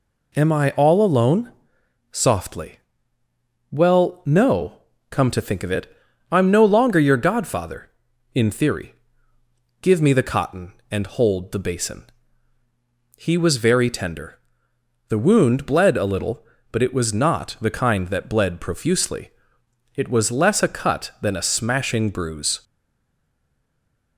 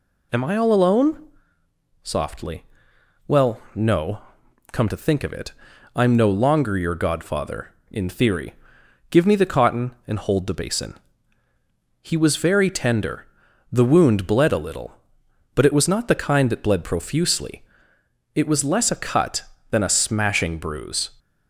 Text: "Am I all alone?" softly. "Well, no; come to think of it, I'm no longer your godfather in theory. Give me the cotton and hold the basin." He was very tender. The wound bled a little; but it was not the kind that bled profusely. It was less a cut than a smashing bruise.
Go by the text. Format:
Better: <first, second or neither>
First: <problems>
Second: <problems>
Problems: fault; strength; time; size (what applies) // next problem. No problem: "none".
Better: second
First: stays silent after the last word; noticeable; from 22.6 s on; 1.5 s long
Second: none